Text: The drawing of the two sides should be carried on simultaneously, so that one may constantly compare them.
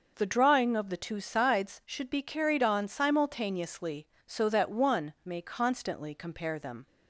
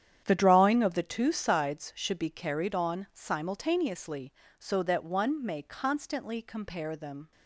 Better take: first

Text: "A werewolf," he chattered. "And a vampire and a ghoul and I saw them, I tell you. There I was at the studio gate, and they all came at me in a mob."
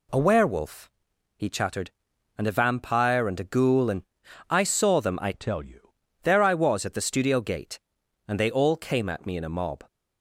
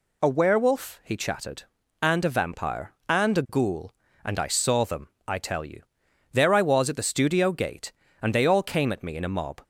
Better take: second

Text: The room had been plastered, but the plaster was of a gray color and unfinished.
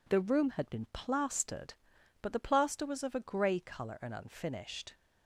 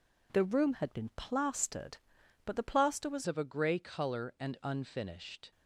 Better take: first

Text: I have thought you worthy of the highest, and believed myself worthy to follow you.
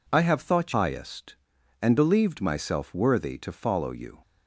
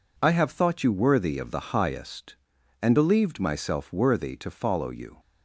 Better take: second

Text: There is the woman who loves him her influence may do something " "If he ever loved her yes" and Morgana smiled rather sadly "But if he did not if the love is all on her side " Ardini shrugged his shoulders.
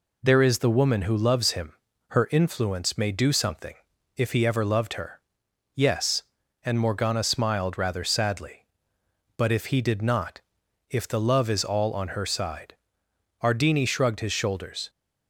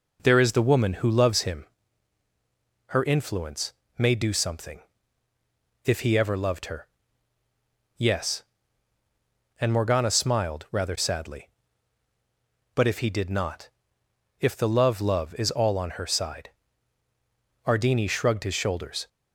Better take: first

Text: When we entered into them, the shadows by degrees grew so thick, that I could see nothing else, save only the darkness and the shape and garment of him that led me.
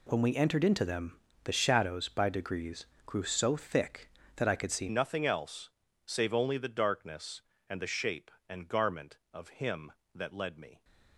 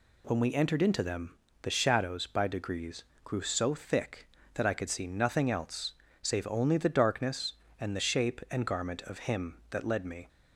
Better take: second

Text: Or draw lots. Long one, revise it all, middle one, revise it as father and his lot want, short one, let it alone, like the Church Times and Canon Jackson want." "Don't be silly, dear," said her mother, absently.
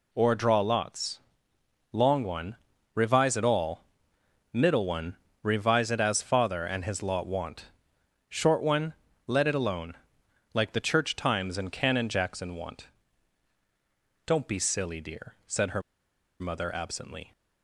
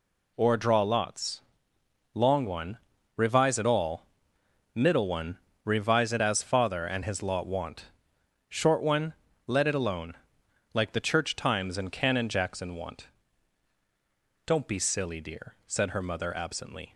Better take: second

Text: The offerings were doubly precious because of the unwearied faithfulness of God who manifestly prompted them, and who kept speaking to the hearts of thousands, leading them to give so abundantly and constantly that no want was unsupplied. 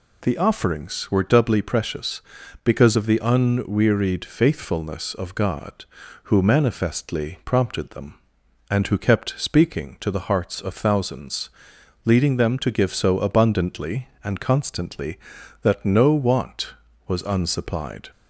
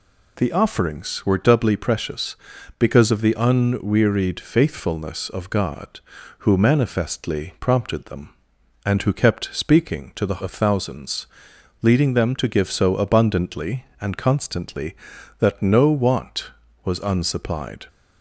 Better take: first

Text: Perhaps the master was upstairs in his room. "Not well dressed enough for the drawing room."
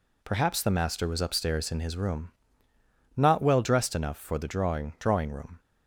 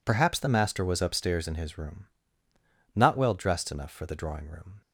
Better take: second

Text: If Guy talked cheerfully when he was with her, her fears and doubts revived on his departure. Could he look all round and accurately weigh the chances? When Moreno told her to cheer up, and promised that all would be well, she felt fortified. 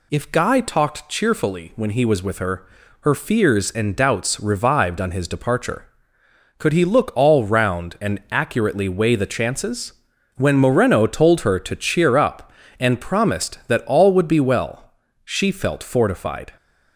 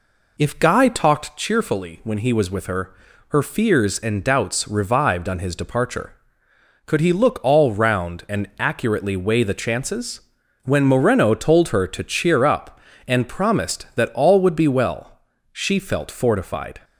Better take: first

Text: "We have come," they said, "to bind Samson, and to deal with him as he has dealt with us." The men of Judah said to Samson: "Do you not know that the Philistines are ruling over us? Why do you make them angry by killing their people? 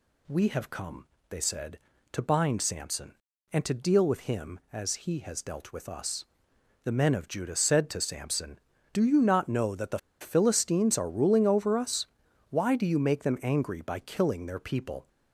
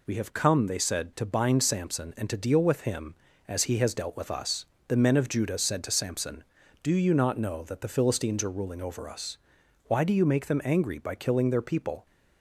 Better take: second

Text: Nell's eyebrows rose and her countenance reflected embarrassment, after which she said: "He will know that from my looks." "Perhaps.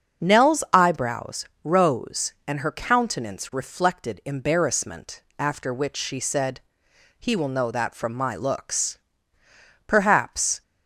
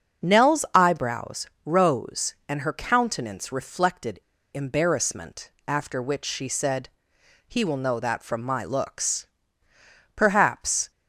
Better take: first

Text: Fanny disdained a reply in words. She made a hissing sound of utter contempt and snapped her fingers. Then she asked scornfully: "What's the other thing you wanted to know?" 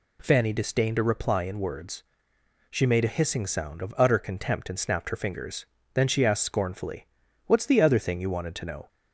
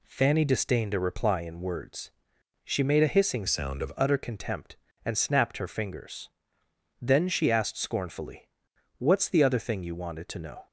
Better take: first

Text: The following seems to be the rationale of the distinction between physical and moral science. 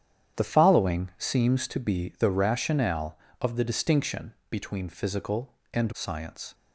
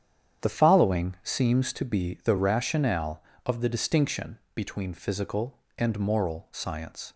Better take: second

